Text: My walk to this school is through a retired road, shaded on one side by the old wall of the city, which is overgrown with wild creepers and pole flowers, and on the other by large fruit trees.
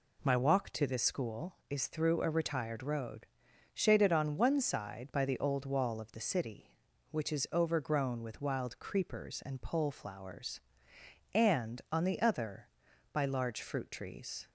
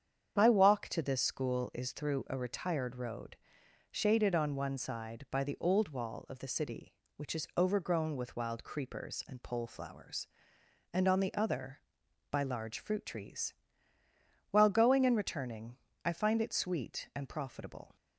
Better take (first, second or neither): first